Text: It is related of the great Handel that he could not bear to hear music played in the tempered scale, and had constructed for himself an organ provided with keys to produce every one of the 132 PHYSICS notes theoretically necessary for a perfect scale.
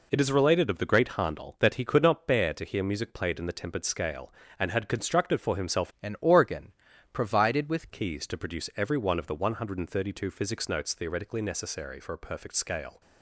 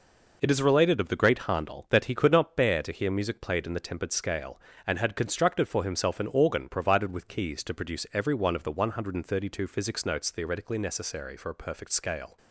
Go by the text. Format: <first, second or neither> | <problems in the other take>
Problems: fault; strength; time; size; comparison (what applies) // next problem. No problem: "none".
second | changes voice from "an" to "with"; from 6.0 to 7.8 s; 1.8 s long // pauses between "organ" and "provided"; at 6.7 s; 0.40 s long